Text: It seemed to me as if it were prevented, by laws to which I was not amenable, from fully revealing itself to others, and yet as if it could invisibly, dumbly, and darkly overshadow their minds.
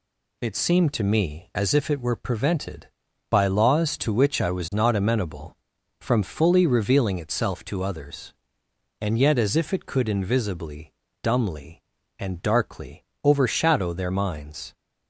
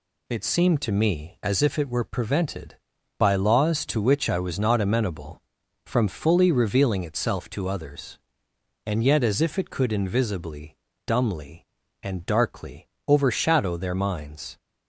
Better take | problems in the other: neither | pauses between "darkly" and "overshadow"; slight; the same in both

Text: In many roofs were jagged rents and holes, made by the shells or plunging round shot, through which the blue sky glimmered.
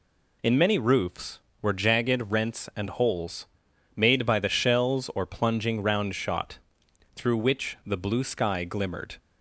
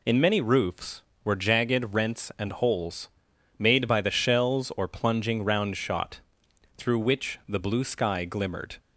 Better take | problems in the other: neither | none

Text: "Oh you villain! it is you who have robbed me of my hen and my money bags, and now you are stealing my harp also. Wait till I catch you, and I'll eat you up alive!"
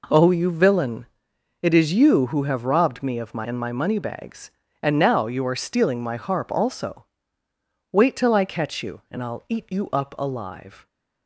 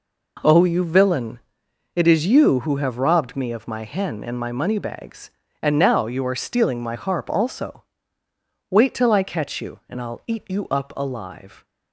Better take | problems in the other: second | skips "hen"; at 3.4 s

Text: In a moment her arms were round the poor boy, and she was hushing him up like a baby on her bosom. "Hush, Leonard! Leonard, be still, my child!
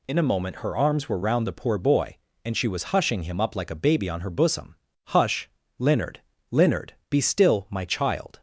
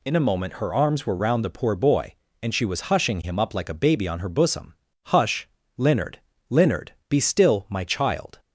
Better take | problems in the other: neither | none

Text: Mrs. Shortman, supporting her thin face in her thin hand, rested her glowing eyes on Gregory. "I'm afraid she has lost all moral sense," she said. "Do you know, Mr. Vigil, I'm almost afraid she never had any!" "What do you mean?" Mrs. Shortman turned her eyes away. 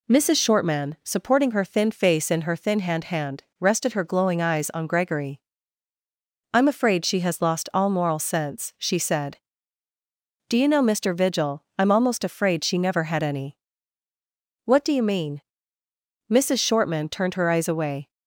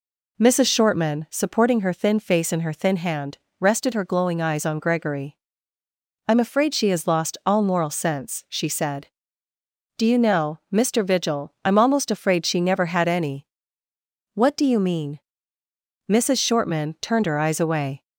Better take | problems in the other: second | says "hand" twice; at 3.0 s

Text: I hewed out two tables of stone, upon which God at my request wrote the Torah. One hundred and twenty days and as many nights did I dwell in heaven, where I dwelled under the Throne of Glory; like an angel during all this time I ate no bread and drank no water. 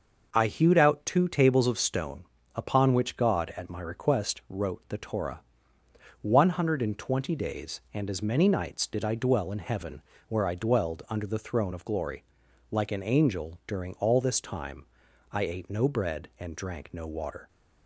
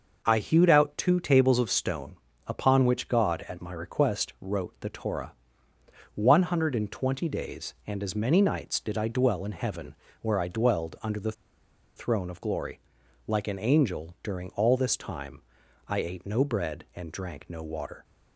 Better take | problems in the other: first | pauses between "the" and "Throne"; noticeable; at 11.3 s; 0.63 s long // pauses between "time" and "I"; noticeable; at 15.3 s; 0.48 s long; noticeable in the first

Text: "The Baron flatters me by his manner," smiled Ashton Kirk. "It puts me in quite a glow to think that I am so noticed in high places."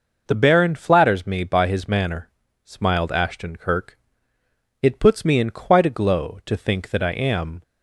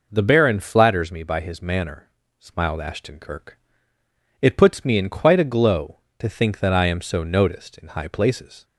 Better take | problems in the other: second | stops before "so noticed in high places"; at 7.6 s

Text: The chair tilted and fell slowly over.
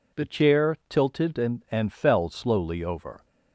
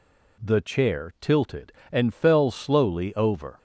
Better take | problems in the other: second | says "and" twice; at 1.7 s

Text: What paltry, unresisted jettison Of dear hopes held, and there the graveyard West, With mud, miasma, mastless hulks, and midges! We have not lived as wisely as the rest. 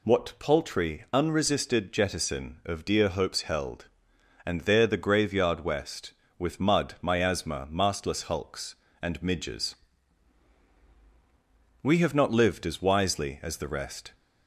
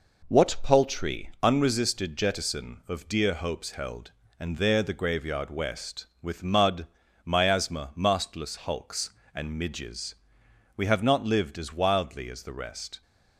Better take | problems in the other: first | says "wildly" for "wisely"; at 11.7 s

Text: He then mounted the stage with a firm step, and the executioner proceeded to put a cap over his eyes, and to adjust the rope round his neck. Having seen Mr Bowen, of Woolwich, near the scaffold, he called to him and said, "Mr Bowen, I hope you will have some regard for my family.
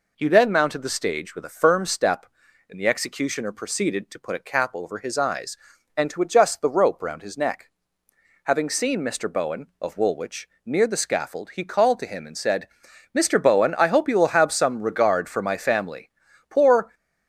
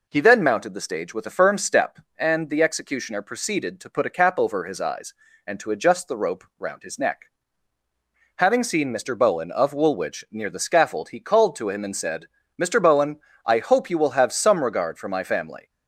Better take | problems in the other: second | goes on to say "Poor"; slight; from 16.4 s on; 0.46 s long

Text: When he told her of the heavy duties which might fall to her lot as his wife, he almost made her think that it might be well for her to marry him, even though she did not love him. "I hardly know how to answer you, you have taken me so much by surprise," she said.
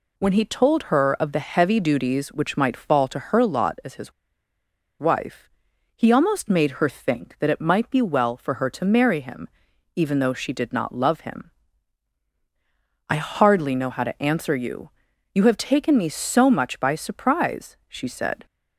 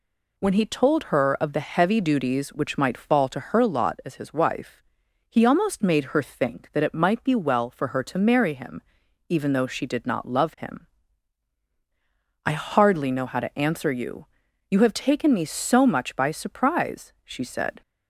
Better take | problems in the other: second | pauses between "his" and "wife"; noticeable; at 4.1 s; 0.87 s long

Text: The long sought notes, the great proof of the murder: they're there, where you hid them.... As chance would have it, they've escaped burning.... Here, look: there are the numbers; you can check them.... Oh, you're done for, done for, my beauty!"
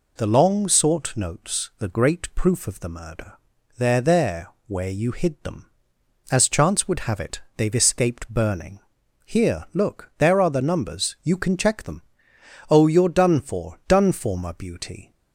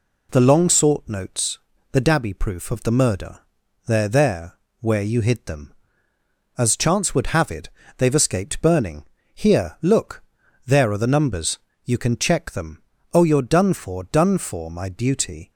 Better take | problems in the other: first | says "dabby" for "great"; at 2.0 s

